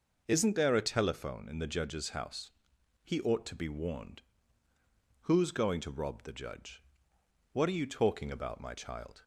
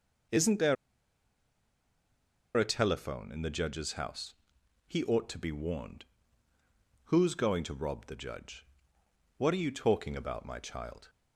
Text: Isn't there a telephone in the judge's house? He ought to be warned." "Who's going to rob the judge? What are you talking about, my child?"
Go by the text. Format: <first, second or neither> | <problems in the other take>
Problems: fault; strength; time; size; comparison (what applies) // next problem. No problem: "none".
first | pauses between "there" and "a"; strong; at 0.7 s; 1.8 s long